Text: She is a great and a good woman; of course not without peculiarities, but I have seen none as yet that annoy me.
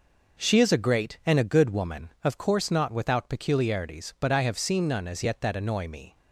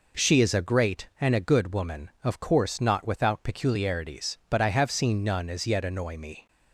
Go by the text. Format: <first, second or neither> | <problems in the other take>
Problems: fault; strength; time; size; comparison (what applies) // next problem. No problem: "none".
first | skips "that"; at 5.8 s